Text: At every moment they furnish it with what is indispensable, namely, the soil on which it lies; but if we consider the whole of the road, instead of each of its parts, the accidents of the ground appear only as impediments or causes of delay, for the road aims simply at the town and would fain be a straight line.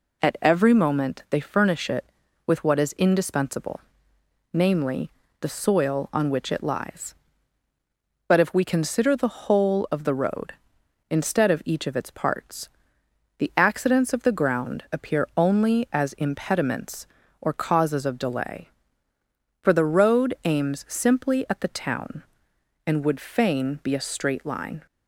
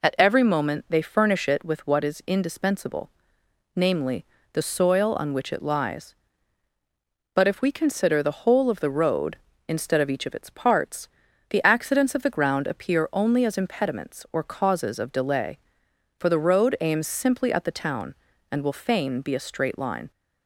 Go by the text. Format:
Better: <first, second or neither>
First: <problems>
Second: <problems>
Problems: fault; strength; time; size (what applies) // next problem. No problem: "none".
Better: first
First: none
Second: says "will" for "would"; at 18.6 s